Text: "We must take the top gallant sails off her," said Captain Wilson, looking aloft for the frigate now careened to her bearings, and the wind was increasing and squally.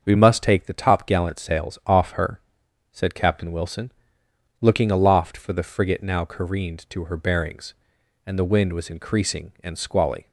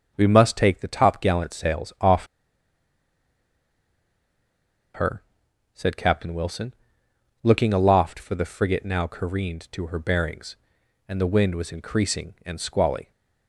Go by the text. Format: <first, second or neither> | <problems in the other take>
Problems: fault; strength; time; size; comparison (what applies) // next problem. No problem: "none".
first | starts louder than the rest; until 1.1 s; 7 dB; also in the first // pauses between "off" and "her"; strong; at 2.2 s; 2.6 s long